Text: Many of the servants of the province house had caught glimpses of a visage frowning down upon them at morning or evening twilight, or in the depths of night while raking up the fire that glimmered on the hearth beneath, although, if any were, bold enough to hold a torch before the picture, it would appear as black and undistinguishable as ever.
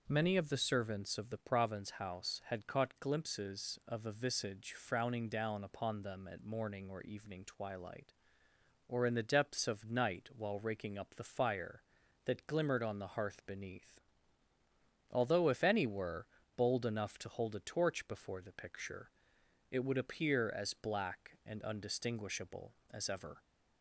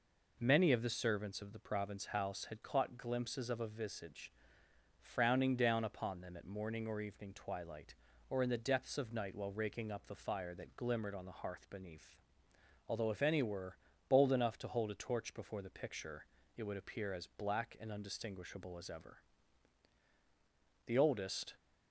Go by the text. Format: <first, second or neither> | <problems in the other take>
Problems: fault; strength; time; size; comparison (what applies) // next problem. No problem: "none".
first | pauses between "visage" and "frowning"; noticeable; at 4.3 s; 0.66 s long // goes on to say "The oldest"; noticeable; from 20.8 s on; 0.68 s long